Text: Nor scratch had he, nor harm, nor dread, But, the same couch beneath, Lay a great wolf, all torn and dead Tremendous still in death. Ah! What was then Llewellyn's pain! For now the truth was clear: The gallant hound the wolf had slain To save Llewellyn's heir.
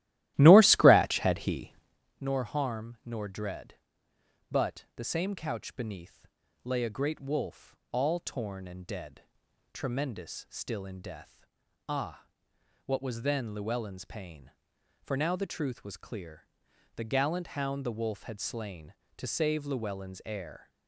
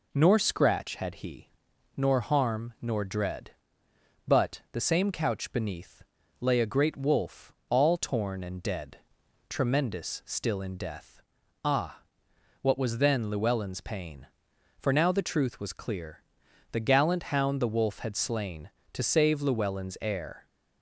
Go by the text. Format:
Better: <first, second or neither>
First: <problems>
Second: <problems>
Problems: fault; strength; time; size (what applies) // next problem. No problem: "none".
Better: second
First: starts louder than the rest; strong; until 2.0 s; 15.5 dB // pauses between "dead" and "Tremendous"; noticeable; at 9.2 s; 0.52 s long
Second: pauses between "dead" and "Tremendous"; noticeable; at 8.9 s; 0.52 s long